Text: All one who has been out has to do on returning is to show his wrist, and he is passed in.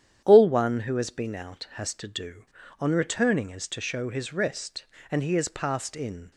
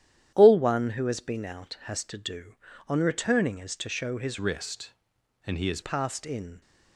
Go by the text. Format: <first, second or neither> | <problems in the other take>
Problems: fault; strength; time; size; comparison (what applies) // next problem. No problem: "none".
first | starts louder than the rest; strong; until 1.3 s; 10.5 dB; strong in the first // changes voice from "wrist" to "is"; from 4.3 to 5.7 s; 1.4 s long